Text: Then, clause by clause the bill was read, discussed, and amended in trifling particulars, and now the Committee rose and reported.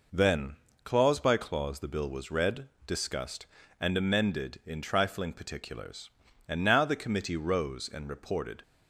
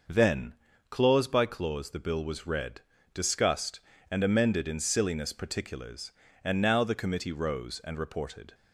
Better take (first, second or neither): first